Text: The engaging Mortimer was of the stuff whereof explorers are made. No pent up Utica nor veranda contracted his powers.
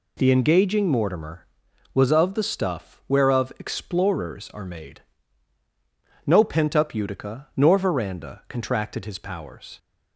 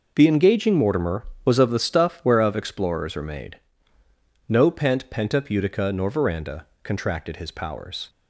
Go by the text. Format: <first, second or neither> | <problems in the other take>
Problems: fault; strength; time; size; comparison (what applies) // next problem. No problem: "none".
first | says "pent" twice; at 5.0 s // pauses between "veranda" and "contracted"; slight; at 6.6 s; 0.18 s long